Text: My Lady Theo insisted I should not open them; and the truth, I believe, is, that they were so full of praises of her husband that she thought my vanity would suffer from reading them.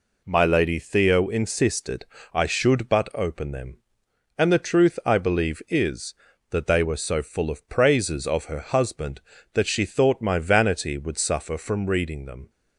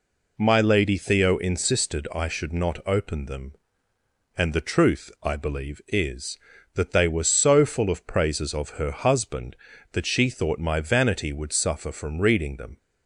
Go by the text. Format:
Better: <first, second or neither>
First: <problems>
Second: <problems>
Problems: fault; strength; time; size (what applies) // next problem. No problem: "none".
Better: second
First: pauses between "insisted" and "I"; slight; at 2.0 s; 0.26 s long // says "but" for "not"; at 2.8 s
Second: none